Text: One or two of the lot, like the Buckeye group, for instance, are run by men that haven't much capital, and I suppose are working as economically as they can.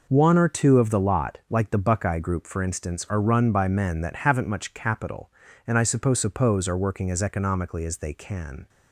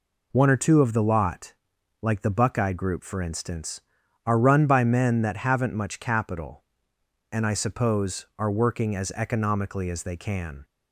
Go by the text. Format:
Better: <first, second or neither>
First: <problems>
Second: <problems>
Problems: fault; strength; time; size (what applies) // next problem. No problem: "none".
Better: second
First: says "suppose" twice; at 6.1 s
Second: none